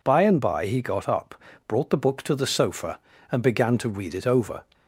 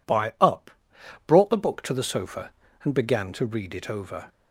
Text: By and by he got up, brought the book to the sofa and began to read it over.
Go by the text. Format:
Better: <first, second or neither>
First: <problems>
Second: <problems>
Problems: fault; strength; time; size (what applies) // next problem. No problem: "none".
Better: first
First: none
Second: skips "and by he got"; at 0.3 s